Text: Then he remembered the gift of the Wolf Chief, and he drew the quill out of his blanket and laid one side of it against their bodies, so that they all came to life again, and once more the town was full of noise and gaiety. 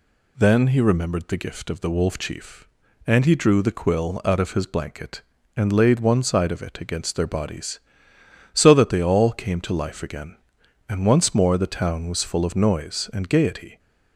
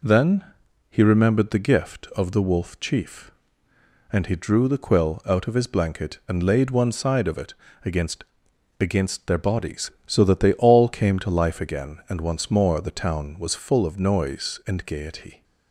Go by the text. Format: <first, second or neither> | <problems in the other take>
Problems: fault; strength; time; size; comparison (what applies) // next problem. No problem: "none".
first | pauses between "Then" and "he"; noticeable; at 0.4 s; 0.48 s long // pauses between "it" and "against"; slight; at 7.5 s; 0.32 s long // says "against" twice; at 8.8 s